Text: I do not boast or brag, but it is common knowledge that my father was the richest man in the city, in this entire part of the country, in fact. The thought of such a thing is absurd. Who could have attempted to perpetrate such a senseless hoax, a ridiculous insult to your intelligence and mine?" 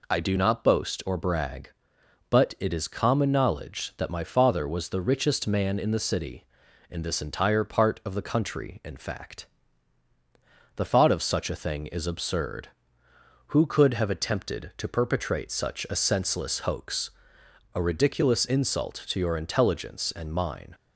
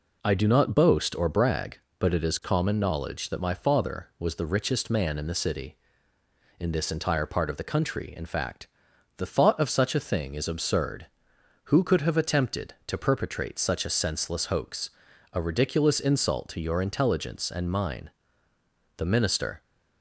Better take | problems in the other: first | goes on to say "The minister"; noticeable; from 18.9 s on; 0.66 s long

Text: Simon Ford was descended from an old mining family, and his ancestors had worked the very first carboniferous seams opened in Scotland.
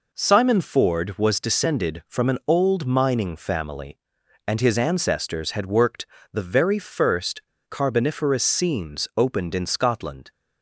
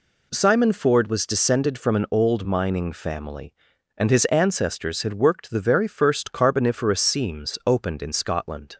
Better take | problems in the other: second | pauses between "worked" and "the"; slight; at 6.0 s; 0.30 s long // pauses between "first" and "carboniferous"; slight; at 7.4 s; 0.27 s long

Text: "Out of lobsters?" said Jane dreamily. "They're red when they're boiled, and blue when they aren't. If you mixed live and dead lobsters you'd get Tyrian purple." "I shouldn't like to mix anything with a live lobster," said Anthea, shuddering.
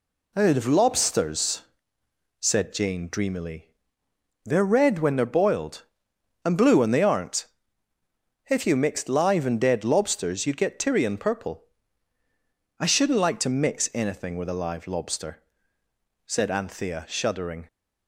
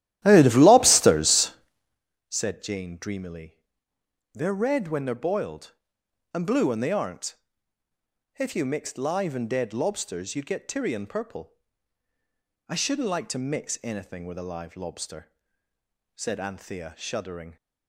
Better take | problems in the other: first | starts louder than the rest; strong; until 2.0 s; 13.5 dB

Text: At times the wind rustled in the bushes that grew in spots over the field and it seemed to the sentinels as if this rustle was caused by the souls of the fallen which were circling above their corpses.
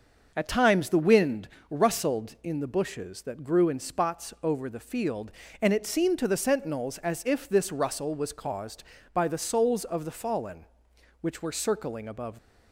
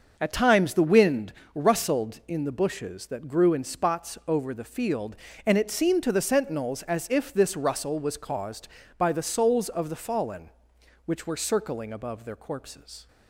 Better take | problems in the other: second | starts louder than the rest; noticeable; until 1.3 s; 6 dB; noticeable in the second // pauses between "wind" and "rustled"; slight; at 1.4 s; 0.20 s long; slight in the second // stops before "their corpses"; at 12.3 s

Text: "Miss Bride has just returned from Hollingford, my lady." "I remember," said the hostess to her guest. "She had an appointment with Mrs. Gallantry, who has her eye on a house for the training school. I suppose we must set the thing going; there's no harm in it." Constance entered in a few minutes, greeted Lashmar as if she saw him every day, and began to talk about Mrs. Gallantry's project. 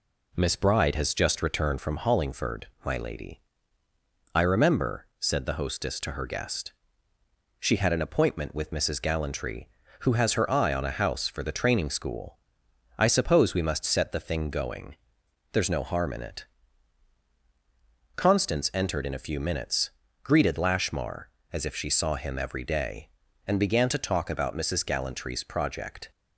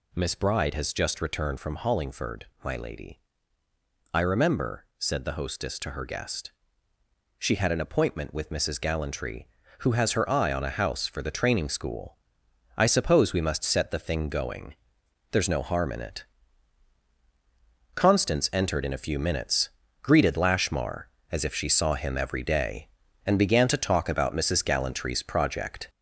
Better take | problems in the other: first | gets louder; noticeable; throughout; 4.5 dB

